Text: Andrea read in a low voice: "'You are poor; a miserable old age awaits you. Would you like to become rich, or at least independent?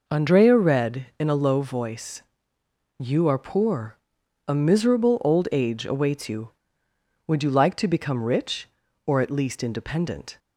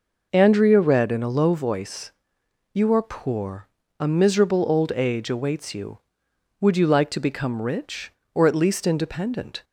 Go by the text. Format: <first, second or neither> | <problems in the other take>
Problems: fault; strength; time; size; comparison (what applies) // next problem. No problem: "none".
neither | none